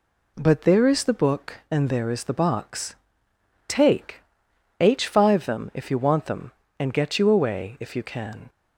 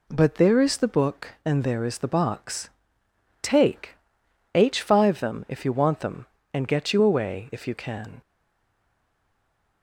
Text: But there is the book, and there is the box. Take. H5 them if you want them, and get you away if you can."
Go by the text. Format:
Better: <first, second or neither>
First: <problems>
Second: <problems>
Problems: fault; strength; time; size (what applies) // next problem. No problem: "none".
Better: first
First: none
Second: stays silent after the last word; noticeable; from 8.2 s on; 1.6 s long